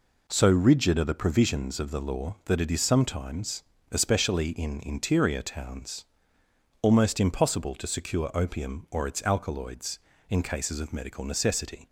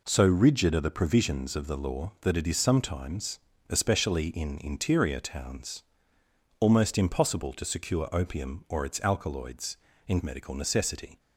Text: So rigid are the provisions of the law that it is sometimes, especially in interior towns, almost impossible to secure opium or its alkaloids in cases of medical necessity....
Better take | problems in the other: first | skips "cases of"; at 10.2 s

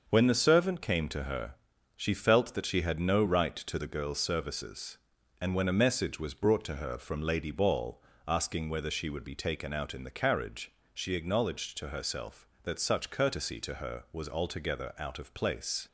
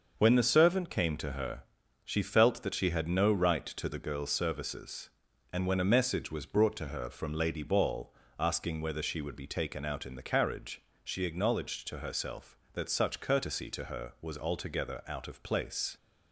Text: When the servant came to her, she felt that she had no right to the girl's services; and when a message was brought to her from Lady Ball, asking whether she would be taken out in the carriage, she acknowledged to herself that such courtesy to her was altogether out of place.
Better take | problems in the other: neither | starts louder than the rest; the same in both

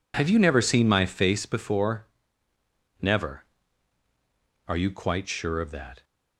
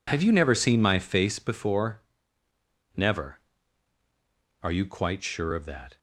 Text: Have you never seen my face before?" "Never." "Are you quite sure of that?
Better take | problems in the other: neither | none

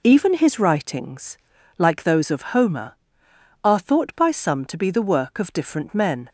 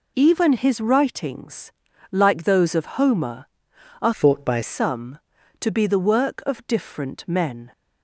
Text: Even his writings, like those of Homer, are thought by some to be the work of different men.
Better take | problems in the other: first | changes voice from "thought" to "by"; from 4.1 to 4.6 s; 0.5 s long

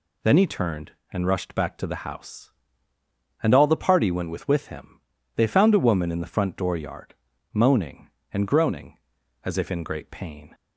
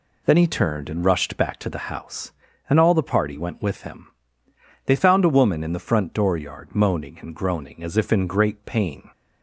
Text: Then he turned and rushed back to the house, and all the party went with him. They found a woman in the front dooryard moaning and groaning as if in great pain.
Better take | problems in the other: second | says "with" twice; at 4.4 s // pauses between "dooryard" and "moaning"; at 7.1 s; 0.38 s long

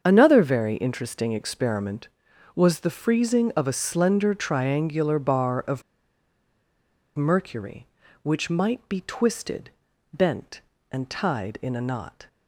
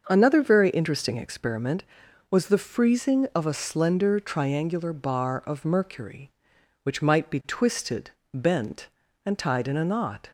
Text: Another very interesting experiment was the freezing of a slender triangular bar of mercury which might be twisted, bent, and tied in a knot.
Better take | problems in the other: second | starts louder than the rest; until 1.0 s; 7 dB; also in the second // pauses between "of" and "mercury"; strong; at 5.8 s; 1.3 s long

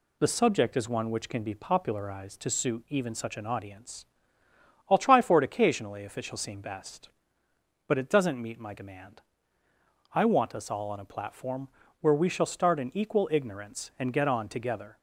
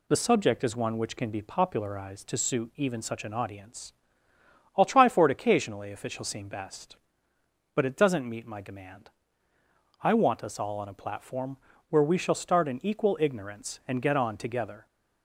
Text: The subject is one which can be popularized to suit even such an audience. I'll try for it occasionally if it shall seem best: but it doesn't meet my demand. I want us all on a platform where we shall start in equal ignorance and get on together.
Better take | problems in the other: neither | pauses between "platform" and "where"; slight; the same in both

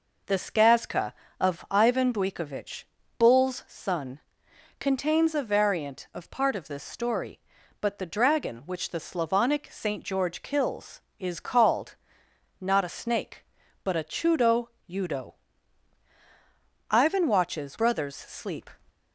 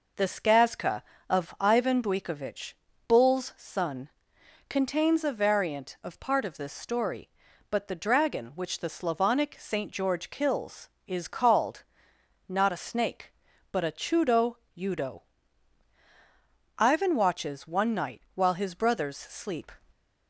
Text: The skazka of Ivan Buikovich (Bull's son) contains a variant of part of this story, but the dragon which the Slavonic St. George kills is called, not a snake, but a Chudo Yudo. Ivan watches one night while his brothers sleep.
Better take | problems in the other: second | pauses between "Chudo" and "Yudo"; slight; at 14.6 s; 0.18 s long; slight in the second // skips "one night while his"; at 17.7 s

